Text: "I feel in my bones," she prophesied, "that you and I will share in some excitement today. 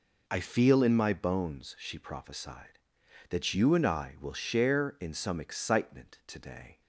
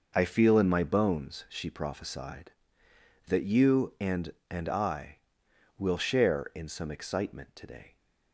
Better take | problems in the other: first | says "and" twice; at 4.4 s

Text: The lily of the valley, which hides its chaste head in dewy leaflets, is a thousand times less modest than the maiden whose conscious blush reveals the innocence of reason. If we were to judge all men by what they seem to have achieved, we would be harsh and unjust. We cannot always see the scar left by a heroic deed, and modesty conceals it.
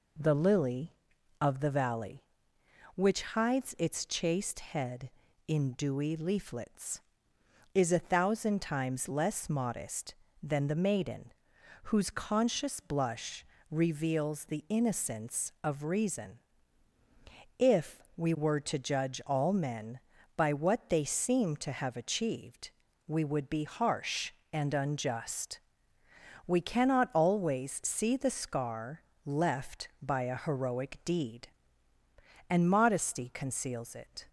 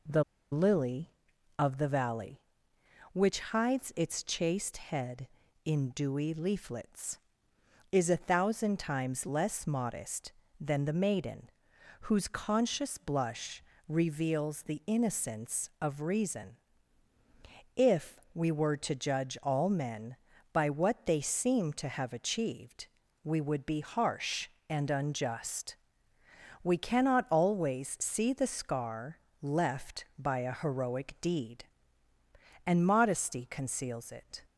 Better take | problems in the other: first | pauses between "The" and "lily"; slight; at 0.2 s; 0.29 s long // pauses between "maiden" and "whose"; noticeable; at 11.5 s; 0.58 s long; noticeable in the first // pauses between "blush" and "reveals"; slight; at 13.6 s; 0.24 s long; slight in the first // pauses between "If" and "we"; slight; at 18.1 s; 0.18 s long; slight in the first // pauses between "scar" and "left"; slight; at 29.1 s; 0.24 s long; slight in the first

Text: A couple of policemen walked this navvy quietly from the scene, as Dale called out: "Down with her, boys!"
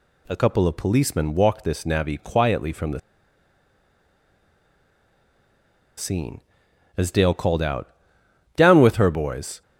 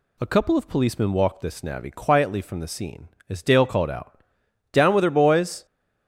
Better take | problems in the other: second | pauses between "the" and "scene"; strong; at 2.9 s; 2.9 s long

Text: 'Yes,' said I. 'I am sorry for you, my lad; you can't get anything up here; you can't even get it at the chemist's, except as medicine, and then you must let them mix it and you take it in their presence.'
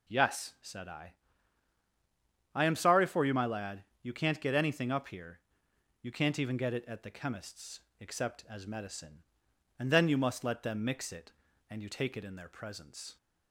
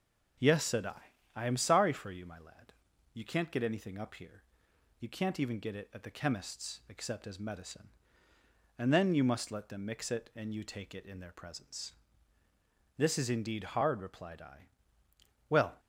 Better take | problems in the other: first | starts louder than the rest; strong; until 1.7 s; 8 dB // goes on to say "This is indeed hard replied I Well"; strong; from 12.9 s on; 2.8 s long

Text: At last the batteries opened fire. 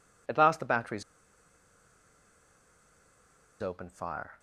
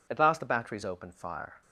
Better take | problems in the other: second | pauses between "batteries" and "opened"; strong; at 1.0 s; 2.5 s long

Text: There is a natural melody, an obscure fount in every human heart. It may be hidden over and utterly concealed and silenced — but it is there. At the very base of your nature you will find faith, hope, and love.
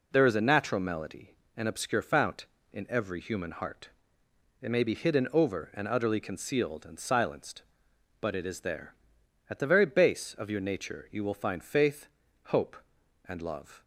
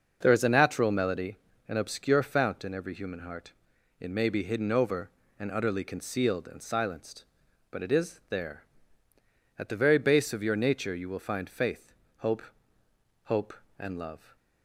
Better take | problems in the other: first | starts louder than the rest; noticeable; until 1.2 s; 6 dB // says "hope" twice; at 13.2 s

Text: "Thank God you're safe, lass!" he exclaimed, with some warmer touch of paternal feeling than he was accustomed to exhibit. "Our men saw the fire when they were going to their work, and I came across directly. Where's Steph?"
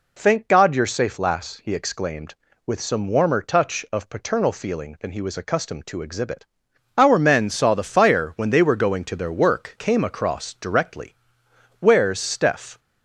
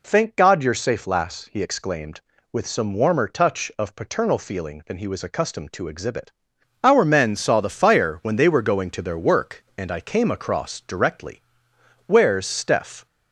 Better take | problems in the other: second | skips "and I"; at 9.7 s

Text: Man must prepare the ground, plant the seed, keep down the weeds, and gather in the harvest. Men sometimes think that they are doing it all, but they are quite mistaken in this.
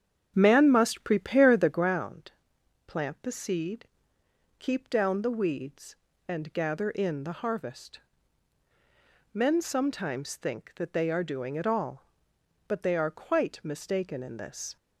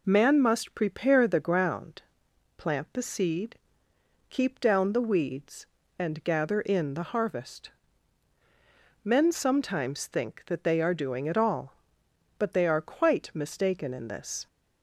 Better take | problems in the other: second | starts louder than the rest; strong; until 2.0 s; 8 dB

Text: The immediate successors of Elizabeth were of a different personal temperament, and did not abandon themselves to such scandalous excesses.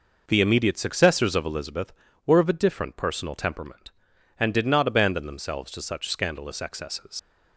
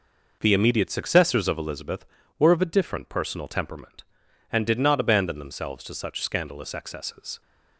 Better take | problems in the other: second | leaves "excesses" unfinished; at 7.1 s; 80 ms

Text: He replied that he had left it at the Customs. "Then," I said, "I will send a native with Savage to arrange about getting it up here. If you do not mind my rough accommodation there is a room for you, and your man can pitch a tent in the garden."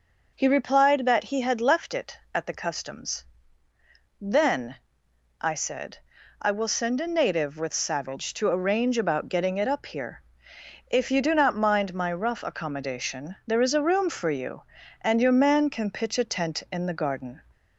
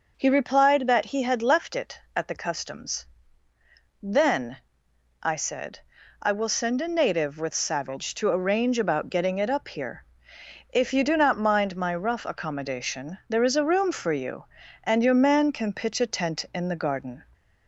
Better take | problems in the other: neither | none

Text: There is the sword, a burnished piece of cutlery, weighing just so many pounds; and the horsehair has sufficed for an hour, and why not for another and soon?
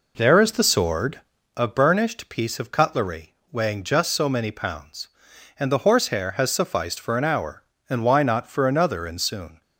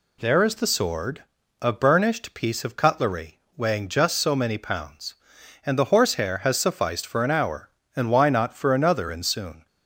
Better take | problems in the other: second | starts louder than the rest; noticeable; until 1.5 s; 4 dB

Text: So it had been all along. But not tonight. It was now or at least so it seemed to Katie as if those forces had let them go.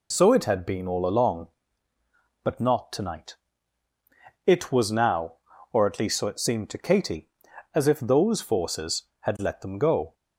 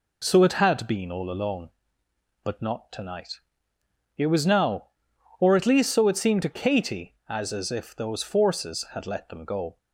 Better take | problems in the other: first | says "as" twice; at 7.5 s

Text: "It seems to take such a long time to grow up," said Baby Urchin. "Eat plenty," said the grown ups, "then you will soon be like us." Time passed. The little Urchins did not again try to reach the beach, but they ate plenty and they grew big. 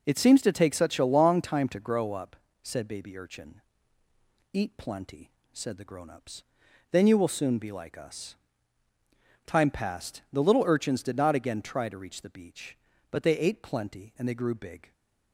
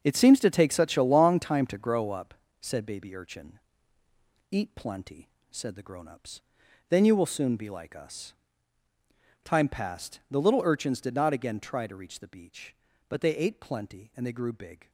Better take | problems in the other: first | gets quieter; strong; throughout; 10 dB

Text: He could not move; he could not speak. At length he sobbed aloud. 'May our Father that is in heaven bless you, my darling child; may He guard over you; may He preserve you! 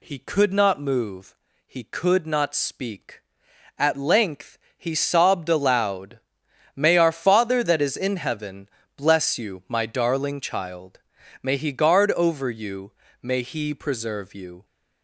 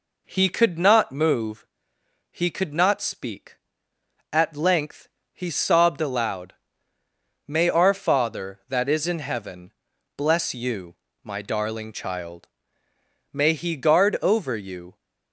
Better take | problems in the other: first | pauses between "length" and "he"; slight; at 5.0 s; 0.26 s long; slight in the first // pauses between "heaven" and "bless"; noticeable; at 9.7 s; 0.46 s long; slight in the first // stops before "may He preserve you"; at 14.9 s

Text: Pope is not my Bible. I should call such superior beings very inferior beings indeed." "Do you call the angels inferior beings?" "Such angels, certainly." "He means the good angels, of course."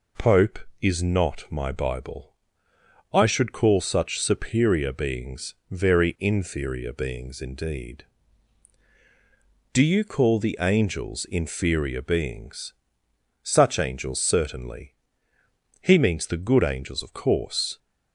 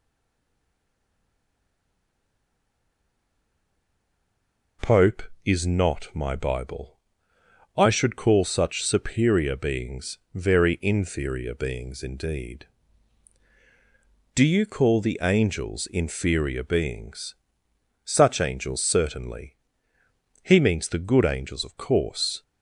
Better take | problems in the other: first | stays silent before the first word; strong; until 4.7 s; 4.7 s long // pauses between "beings" and "very"; slight; at 10.1 s; 0.16 s long; slight in the first

